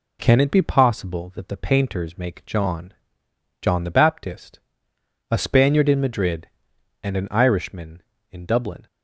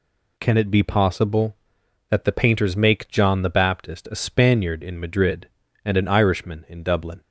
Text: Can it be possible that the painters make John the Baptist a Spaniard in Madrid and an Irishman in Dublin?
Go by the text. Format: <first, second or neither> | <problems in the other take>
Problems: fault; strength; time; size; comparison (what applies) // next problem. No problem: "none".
second | says "John" twice; at 3.6 s // pauses between "Baptist" and "a"; noticeable; at 4.5 s; 0.72 s long